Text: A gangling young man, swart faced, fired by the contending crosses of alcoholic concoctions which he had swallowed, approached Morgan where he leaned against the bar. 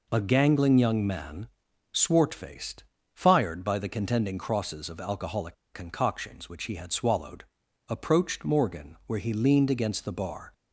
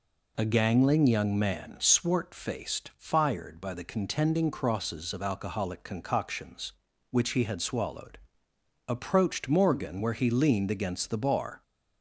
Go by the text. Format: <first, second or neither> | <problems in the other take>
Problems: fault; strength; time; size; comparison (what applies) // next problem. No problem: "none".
second | pauses between "alcoholic" and "concoctions"; slight; at 5.5 s; 0.20 s long